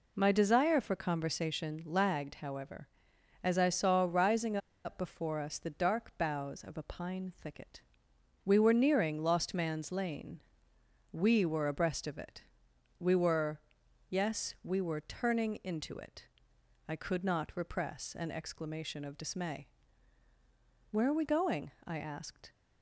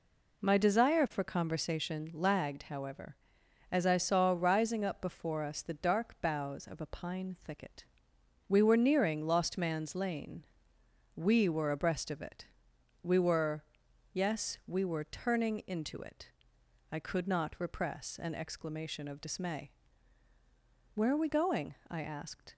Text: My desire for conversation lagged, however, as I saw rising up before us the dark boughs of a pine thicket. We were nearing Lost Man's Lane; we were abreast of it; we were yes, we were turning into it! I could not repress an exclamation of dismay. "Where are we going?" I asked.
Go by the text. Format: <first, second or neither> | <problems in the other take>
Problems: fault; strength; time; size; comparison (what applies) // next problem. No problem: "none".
second | pauses between "rising" and "up"; slight; at 4.5 s; 0.27 s long // pauses between "were" and "yes"; noticeable; at 13.5 s; 0.50 s long; noticeable in the second